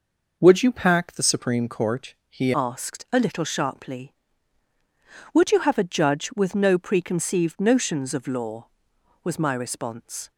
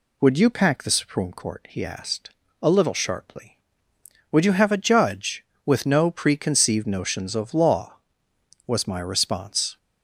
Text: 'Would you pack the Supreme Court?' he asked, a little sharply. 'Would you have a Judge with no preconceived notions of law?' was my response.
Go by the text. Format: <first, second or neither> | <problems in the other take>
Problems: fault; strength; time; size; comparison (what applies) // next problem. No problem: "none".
second | changes voice at "asked"; from 2.5 s on; 7.8 s long